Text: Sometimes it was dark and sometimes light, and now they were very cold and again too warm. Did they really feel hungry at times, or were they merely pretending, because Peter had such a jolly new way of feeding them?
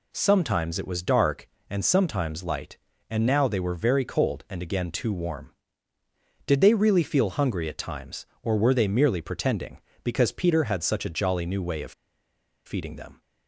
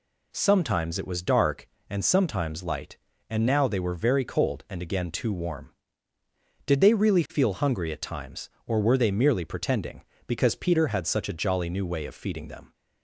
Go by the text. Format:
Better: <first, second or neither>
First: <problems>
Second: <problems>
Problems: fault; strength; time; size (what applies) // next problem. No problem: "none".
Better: second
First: pauses between "of" and "feeding"; noticeable; at 11.9 s; 0.74 s long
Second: none